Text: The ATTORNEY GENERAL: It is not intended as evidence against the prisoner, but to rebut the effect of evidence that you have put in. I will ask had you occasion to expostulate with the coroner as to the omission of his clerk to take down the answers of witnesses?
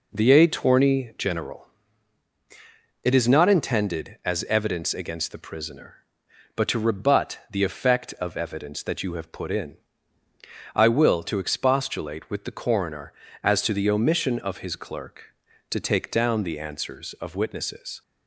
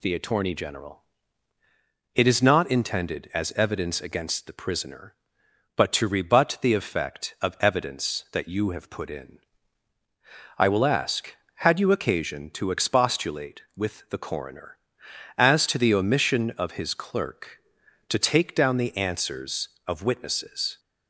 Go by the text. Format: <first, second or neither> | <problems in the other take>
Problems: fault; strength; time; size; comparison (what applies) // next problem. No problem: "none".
second | skips "ask had you occasion"; at 11.2 s